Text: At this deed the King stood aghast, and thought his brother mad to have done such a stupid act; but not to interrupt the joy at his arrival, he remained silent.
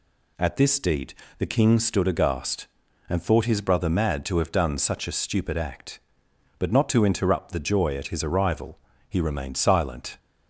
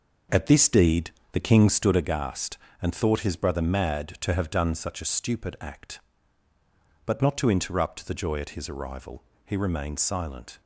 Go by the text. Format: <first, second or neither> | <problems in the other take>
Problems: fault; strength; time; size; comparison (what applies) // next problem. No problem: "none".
first | starts louder than the rest; noticeable; until 2.1 s; 6 dB // pauses between "deed" and "the"; slight; at 1.0 s; 0.22 s long; slight in the first